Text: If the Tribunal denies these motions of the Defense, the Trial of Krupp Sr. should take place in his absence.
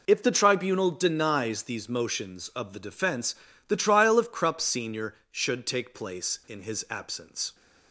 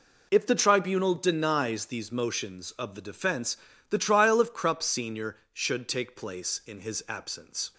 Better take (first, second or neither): neither